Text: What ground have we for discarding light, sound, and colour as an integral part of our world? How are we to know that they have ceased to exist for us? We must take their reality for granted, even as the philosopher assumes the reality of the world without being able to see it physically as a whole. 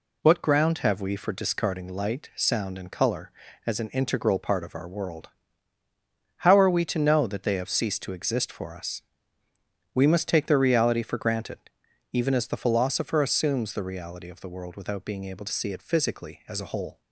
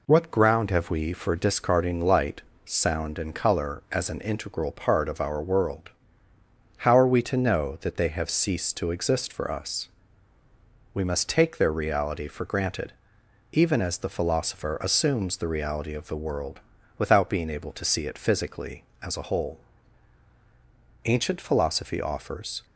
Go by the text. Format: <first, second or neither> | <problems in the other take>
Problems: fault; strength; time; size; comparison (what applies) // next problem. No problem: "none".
first | pauses between "world" and "without"; at 16.5 s; 0.40 s long // goes on to say "Ancient philosophy offers"; from 21.0 s on; 1.6 s long